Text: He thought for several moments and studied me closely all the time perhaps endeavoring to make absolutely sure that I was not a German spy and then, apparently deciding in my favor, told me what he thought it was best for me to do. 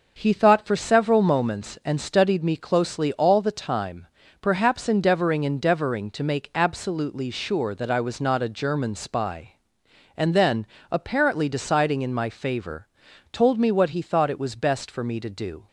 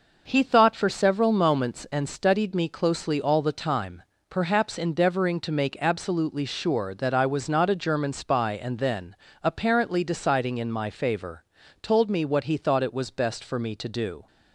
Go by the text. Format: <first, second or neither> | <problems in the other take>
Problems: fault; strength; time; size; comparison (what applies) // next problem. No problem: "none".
second | starts louder than the rest; until 1.1 s; 6.5 dB // pauses between "time" and "perhaps"; slight; at 4.0 s; 0.34 s long; slight in the second // says "endeavoring" twice; at 5.4 s